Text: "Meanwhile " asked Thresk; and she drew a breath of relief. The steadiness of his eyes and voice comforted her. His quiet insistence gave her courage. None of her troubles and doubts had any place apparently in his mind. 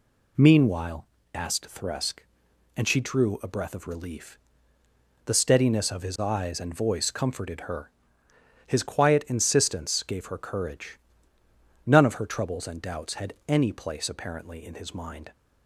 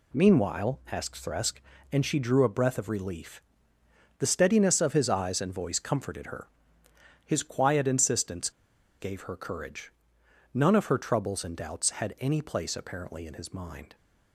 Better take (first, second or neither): first